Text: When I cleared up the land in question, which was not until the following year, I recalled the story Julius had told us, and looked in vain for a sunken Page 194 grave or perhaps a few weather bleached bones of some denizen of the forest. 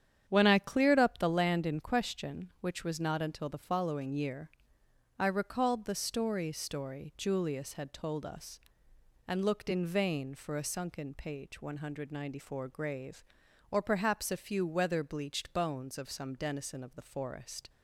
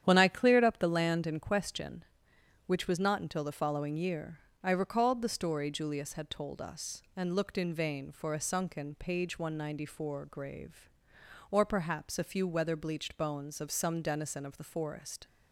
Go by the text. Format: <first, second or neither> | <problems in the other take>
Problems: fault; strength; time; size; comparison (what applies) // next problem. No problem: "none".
second | starts louder than the rest; strong; until 1.2 s; 9 dB; strong in the second // says "story" twice; at 6.5 s